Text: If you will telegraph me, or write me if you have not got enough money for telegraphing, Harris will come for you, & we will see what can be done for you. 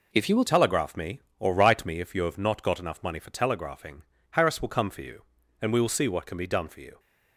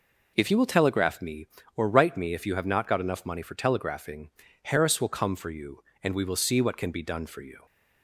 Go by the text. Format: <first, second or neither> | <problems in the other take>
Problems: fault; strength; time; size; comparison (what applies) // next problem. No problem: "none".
second | changes voice at "telegraph"; from 0.4 s on; 6.5 s long